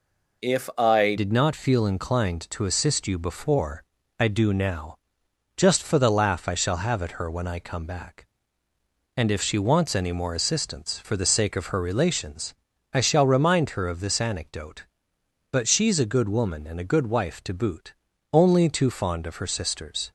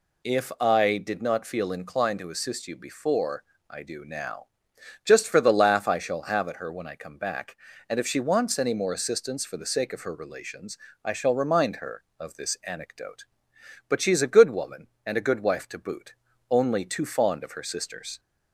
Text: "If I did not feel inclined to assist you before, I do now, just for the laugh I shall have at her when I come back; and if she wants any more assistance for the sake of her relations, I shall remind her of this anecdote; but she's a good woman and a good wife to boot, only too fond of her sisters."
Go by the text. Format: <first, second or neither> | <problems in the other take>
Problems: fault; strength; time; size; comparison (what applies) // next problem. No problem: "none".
second | changes voice at "did"; from 1.1 s on; 19.0 s long